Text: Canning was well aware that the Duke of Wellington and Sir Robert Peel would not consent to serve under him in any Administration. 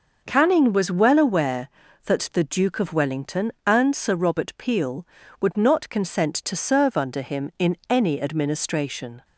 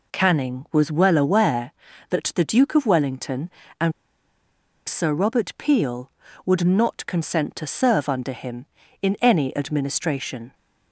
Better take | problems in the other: first | pauses between "and" and "Sir"; noticeable; at 3.9 s; 0.96 s long

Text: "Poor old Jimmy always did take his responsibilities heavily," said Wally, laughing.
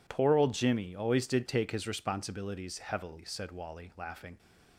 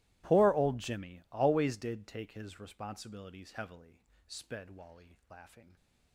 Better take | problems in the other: first | starts louder than the rest; strong; until 1.3 s; 18 dB // says "sped" for "said"; at 4.2 s

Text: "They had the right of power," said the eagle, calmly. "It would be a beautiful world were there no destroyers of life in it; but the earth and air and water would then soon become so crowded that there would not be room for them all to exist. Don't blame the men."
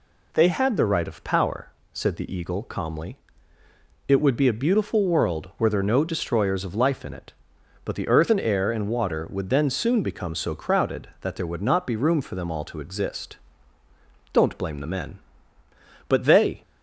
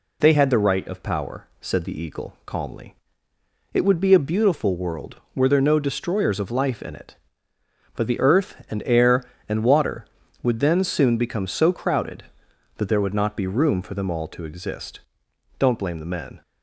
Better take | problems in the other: second | goes on to say "But they"; from 16.0 s on; 0.54 s long

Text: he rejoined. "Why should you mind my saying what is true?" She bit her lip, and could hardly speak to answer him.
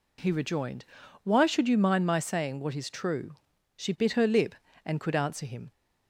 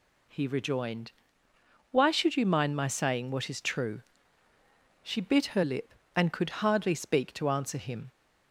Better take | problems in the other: second | skips "hardly speak to"; at 5.1 s

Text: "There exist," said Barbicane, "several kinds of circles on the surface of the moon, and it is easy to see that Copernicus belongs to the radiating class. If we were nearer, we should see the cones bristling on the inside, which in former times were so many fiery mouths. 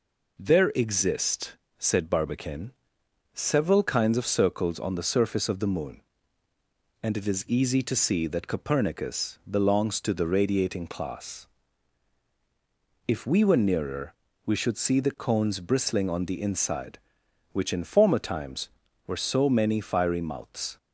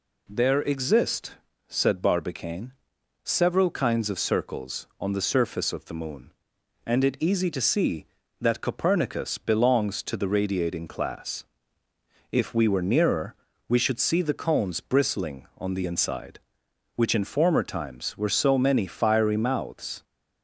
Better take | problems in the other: first | skips "is"; at 7.1 s

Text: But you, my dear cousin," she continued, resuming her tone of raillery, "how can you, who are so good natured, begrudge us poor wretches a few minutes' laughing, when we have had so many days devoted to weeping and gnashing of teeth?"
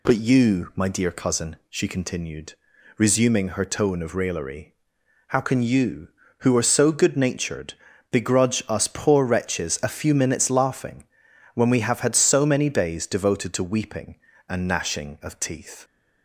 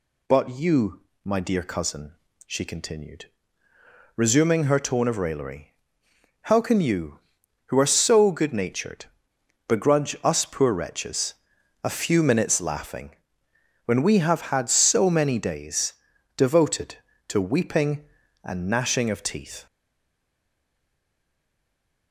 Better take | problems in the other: first | pauses between "wretches" and "a"; noticeable; at 11.3 s; 0.48 s long // pauses between "days" and "devoted"; at 15.9 s; 0.42 s long // stays silent after the last word; from 19.6 s on; 2.5 s long

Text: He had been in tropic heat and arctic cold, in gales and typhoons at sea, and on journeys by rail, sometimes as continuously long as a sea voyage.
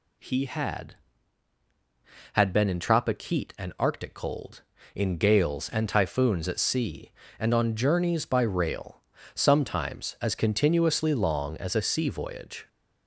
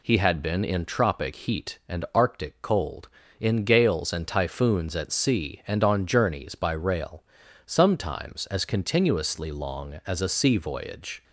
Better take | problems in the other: second | says "had" twice; at 2.3 s

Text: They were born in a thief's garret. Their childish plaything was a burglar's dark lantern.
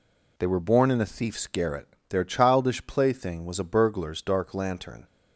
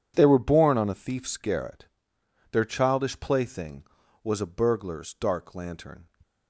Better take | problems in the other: first | says "on" for "in"; at 0.7 s

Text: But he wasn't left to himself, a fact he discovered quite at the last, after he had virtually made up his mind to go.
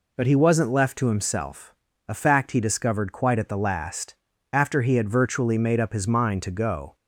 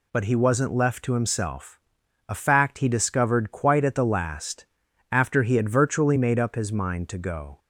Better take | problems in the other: neither | none

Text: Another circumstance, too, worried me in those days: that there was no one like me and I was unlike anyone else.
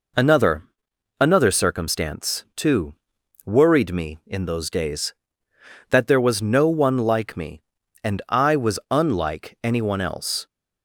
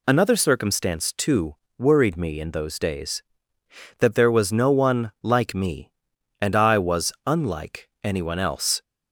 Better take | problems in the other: second | says "Another" twice; at 1.1 s

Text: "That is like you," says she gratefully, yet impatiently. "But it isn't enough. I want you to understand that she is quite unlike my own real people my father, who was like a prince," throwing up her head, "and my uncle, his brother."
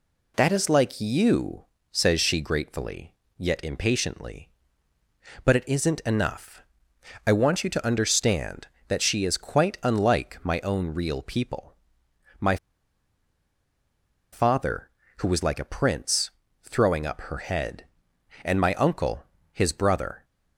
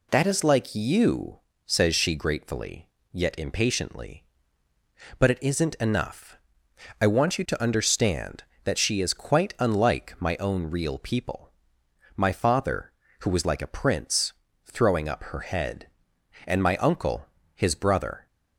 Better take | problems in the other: second | pauses between "people" and "my"; noticeable; at 11.7 s; 0.70 s long; noticeable in the second // pauses between "my" and "father"; strong; at 12.5 s; 1.7 s long

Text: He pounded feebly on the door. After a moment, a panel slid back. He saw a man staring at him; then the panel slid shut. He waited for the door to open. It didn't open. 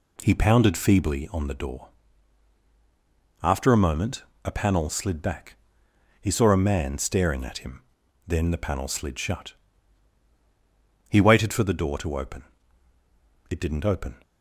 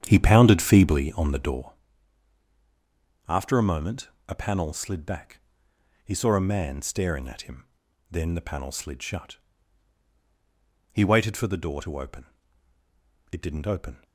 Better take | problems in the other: first | starts louder than the rest; strong; until 1.8 s; 9 dB

